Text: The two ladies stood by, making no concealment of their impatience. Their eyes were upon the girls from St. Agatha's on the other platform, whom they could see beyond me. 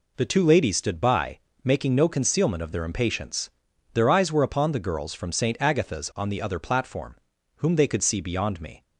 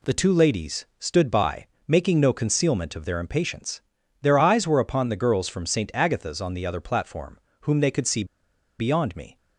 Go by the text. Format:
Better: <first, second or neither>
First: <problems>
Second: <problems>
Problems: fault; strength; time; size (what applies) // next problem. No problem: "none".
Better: first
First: none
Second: pauses between "see" and "beyond"; noticeable; at 8.2 s; 0.54 s long